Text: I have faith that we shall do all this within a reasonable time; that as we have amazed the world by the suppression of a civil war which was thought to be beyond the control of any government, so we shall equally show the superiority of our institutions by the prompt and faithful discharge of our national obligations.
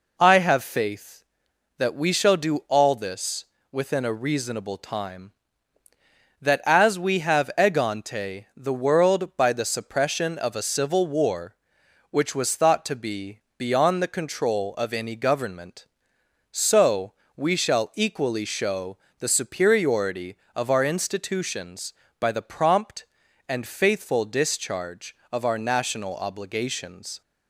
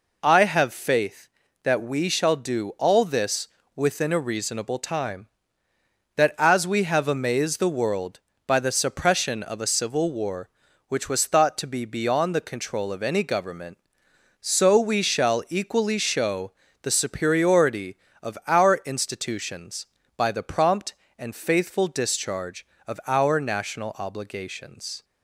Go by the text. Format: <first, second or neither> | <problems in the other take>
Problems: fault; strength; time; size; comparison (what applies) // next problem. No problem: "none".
second | pauses between "this" and "within"; slight; at 3.4 s; 0.26 s long; slight in the second // says "egante" for "amazed"; at 7.5 s // pauses between "be" and "beyond"; slight; at 13.4 s; 0.18 s long // pauses between "so" and "we"; slight; at 17.1 s; 0.22 s long // pauses between "show" and "the"; slight; at 18.9 s; 0.22 s long; slight in the second